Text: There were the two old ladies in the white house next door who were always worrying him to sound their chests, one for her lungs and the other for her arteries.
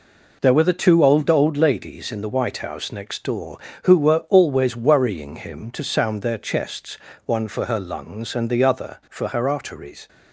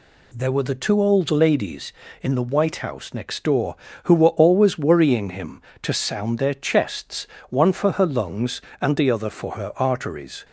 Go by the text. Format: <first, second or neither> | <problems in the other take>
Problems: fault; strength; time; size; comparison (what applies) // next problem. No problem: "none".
second | says "old" twice; at 1.2 s